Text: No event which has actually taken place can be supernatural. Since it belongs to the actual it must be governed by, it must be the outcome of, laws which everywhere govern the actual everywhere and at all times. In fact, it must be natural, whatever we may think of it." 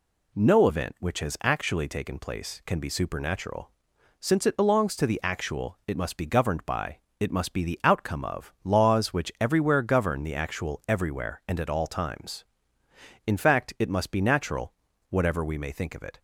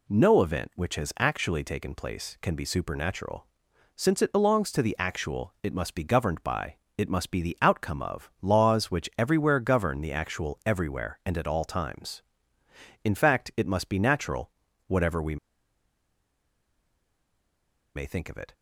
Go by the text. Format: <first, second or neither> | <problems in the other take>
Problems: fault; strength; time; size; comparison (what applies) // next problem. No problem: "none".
first | pauses between "we" and "may"; strong; at 15.3 s; 2.5 s long